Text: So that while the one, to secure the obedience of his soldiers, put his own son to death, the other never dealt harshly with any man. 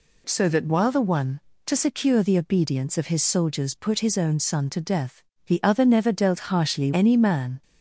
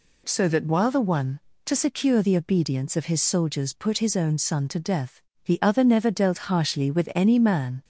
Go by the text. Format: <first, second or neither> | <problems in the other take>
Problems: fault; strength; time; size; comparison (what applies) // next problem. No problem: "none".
second | skips "with"; at 6.9 s